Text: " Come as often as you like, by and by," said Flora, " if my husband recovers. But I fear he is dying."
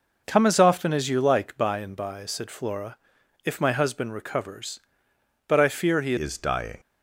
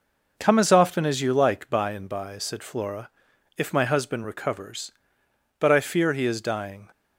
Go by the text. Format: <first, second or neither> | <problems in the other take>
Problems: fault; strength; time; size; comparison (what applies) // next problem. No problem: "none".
second | changes voice at "is"; from 6.1 s on; 0.6 s long